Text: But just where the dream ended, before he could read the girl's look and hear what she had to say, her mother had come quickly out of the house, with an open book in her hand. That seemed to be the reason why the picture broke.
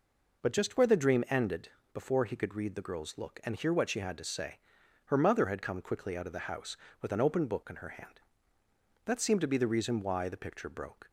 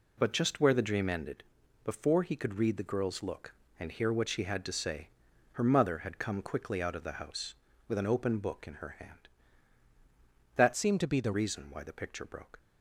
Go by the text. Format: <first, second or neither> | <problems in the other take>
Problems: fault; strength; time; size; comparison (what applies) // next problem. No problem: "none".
first | changes voice from "seemed" to "the"; from 10.7 to 11.3 s; 0.6 s long